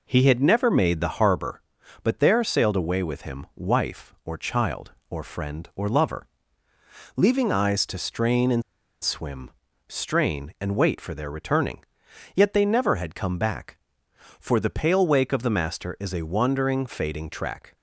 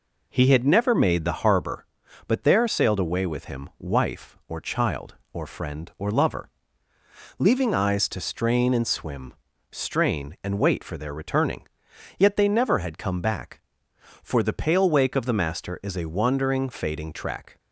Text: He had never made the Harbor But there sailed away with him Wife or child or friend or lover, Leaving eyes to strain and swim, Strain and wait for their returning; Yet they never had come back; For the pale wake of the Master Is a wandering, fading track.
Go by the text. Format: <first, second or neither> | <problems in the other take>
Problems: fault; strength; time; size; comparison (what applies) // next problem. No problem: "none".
second | pauses between "and" and "swim"; at 8.6 s; 0.41 s long